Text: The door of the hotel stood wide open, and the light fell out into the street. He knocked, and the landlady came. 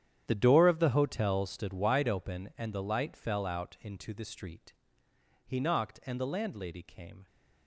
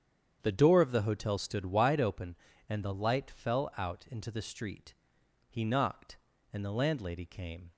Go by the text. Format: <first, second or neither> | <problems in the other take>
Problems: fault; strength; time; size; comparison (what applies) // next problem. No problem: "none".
second | gets quieter; strong; throughout; 15.5 dB // starts louder than the rest; strong; until 1.3 s; 10 dB; strong in the second